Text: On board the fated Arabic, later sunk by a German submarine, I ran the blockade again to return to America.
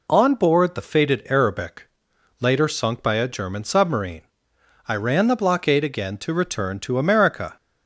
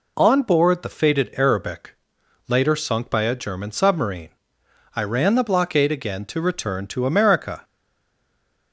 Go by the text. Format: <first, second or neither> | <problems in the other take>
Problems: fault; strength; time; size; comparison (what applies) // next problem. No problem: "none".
first | stays silent after the last word; from 7.6 s on; 1.1 s long